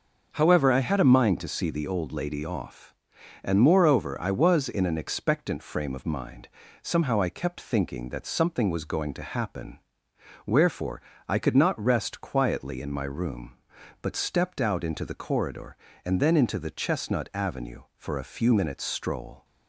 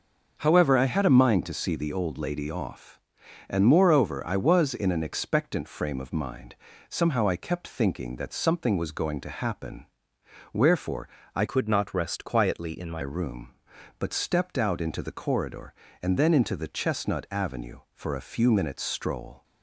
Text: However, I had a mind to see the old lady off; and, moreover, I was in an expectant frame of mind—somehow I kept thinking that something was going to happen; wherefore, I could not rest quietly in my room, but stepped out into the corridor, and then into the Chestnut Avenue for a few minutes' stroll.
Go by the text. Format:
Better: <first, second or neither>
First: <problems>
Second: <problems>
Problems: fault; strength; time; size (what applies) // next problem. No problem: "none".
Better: first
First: starts louder than the rest; until 1.3 s; 6 dB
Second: starts louder than the rest; noticeable; until 1.3 s; 6 dB // changes voice from "could" to "my"; from 11.4 to 13.0 s; 1.6 s long